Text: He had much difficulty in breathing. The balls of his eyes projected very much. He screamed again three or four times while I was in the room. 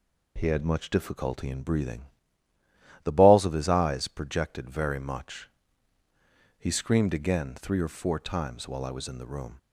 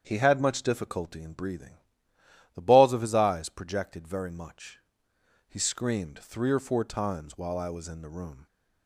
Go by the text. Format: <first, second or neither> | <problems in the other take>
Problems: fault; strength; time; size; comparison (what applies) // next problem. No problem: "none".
first | starts louder than the rest; strong; until 1.0 s; 8 dB // skips "again"; at 6.1 s